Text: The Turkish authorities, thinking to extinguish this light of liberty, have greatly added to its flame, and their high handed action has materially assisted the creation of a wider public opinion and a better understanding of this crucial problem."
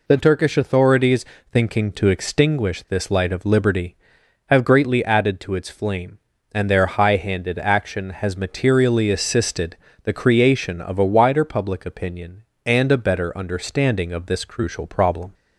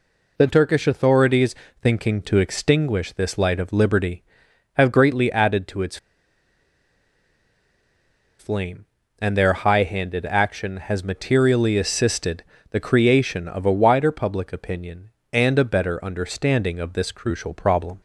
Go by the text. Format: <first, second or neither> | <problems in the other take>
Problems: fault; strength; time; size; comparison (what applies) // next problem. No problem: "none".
first | pauses between "its" and "flame"; strong; at 5.9 s; 2.4 s long // pauses between "assisted" and "the"; slight; at 12.4 s; 0.28 s long; slight in the first